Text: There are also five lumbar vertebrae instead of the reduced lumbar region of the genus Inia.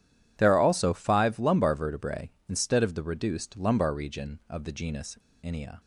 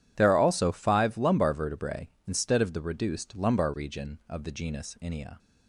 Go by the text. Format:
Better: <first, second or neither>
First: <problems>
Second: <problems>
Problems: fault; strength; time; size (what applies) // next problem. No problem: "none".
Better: second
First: pauses between "genus" and "Inia"; slight; at 5.1 s; 0.27 s long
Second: none